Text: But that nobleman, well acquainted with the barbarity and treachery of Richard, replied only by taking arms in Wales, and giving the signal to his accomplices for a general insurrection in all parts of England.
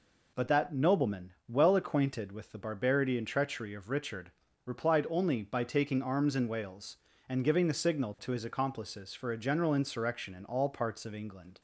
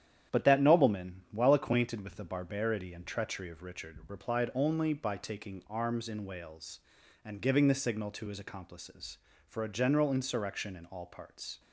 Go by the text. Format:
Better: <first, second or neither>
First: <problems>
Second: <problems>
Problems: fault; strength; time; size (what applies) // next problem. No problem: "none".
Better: first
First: none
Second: starts louder than the rest; strong; until 1.4 s; 9.5 dB // stops before "of England"; at 11.5 s